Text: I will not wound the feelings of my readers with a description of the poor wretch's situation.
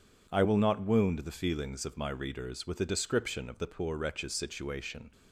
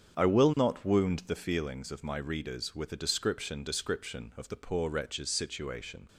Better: first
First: none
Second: starts louder than the rest; strong; until 1.2 s; 8 dB // says "description" twice; at 3.6 s

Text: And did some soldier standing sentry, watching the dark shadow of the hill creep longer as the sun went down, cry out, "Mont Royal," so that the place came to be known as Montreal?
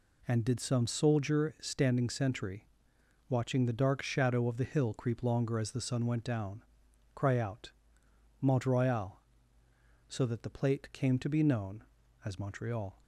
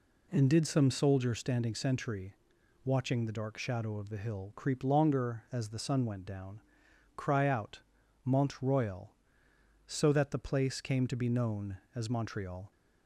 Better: second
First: says "plate" for "place"; at 10.5 s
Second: none

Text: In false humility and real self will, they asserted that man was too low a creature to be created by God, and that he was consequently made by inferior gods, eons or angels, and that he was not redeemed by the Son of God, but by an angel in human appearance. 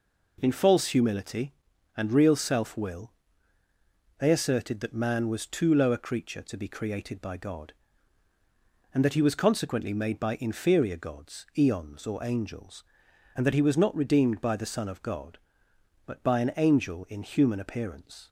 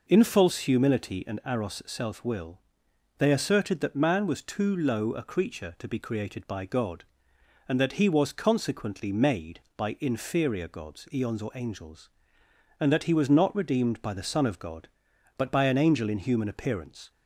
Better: first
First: none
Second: says "aros" for "real"; at 1.4 s

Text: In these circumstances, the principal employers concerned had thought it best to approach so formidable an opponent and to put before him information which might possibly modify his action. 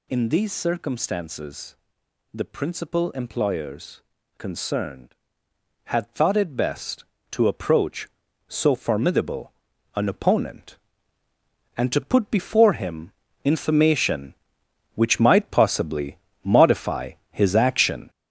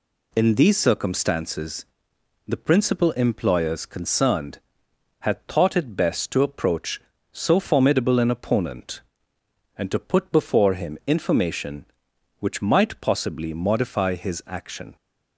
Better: second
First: gets louder; throughout; 6.5 dB // pauses between "employers" and "concerned"; slight; at 4.0 s; 0.36 s long // pauses between "formidable" and "an"; at 9.5 s; 0.44 s long // pauses between "him" and "information"; slight; at 13.1 s; 0.34 s long // pauses between "possibly" and "modify"; slight; at 16.1 s; 0.26 s long // pauses between "modify" and "his"; slight; at 17.1 s; 0.20 s long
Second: none

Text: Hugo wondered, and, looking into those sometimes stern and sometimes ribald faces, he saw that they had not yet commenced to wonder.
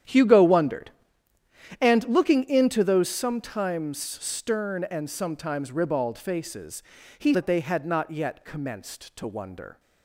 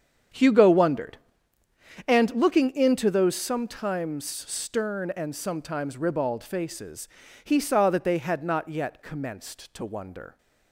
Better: second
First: starts louder than the rest; strong; until 1.9 s; 10 dB // skips "saw"; at 7.3 s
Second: starts louder than the rest; strong; until 2.2 s; 8 dB

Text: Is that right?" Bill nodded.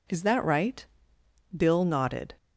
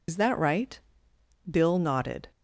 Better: first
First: none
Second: loses the start of "Is"; at 0.0 s; 55 ms

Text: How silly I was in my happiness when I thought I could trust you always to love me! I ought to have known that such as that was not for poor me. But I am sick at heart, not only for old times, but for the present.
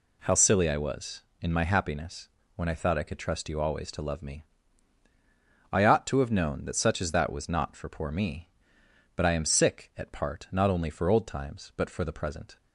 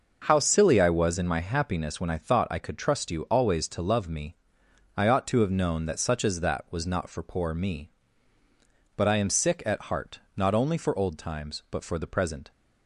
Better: second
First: pauses between "happiness" and "when"; slight; at 2.2 s; 0.26 s long // says "part" for "heart"; at 10.1 s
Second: none

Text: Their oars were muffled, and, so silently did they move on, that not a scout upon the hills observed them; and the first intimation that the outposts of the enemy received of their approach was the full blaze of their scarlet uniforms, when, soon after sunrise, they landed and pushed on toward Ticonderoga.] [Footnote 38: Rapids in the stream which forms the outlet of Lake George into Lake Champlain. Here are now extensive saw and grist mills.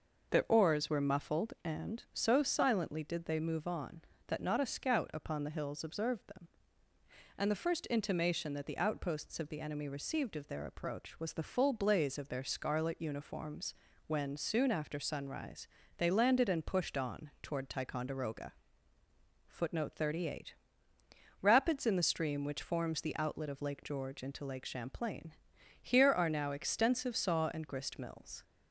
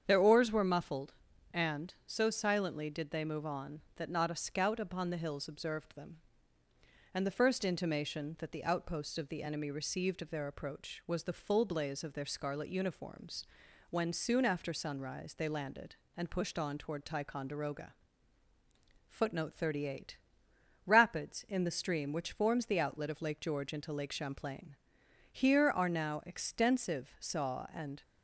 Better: first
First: none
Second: starts louder than the rest; strong; until 1.0 s; 8 dB // stops before "grist mills"; at 28.0 s

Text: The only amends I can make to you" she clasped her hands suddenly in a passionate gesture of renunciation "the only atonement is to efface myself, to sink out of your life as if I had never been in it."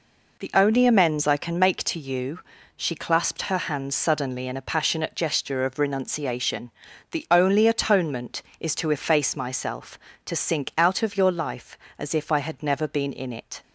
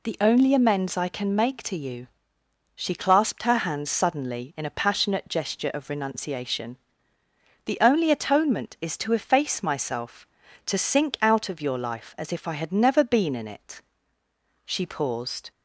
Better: first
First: pauses between "you" and "she"; slight; at 2.3 s; 0.36 s long // pauses between "renunciation" and "the"; at 6.7 s; 0.40 s long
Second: pauses between "you" and "she"; noticeable; at 2.0 s; 0.68 s long // pauses between "renunciation" and "the"; noticeable; at 6.7 s; 0.88 s long // goes on to say "She paused"; noticeable; from 14.6 s on; 0.86 s long

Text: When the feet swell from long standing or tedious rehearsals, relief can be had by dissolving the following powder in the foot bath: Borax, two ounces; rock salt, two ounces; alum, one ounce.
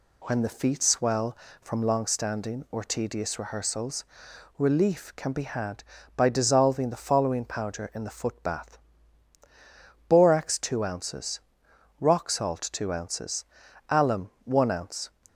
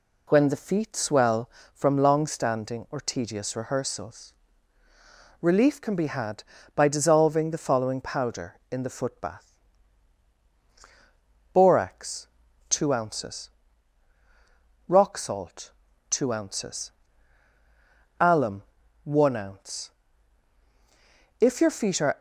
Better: first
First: none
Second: goes on to say "If your feet are"; noticeable; from 21.4 s on; 0.78 s long

